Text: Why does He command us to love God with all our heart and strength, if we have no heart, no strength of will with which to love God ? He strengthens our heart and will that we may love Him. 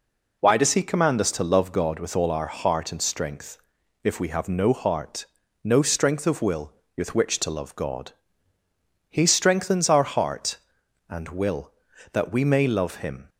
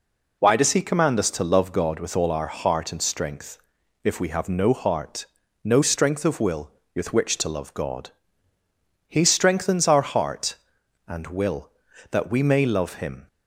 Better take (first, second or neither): neither